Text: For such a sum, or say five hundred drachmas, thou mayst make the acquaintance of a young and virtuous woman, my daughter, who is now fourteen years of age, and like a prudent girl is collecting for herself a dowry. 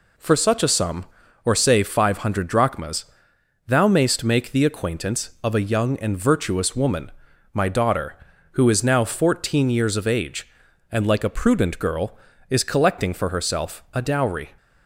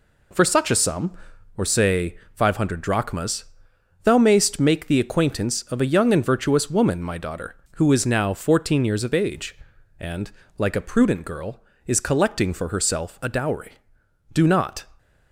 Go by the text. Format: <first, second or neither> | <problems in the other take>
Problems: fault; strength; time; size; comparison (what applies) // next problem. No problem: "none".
first | pauses between "say" and "five"; slight; at 2.1 s; 0.18 s long // pauses between "and" and "like"; slight; at 10.3 s; 0.26 s long // goes on to say "Do not"; from 14.3 s on; 0.54 s long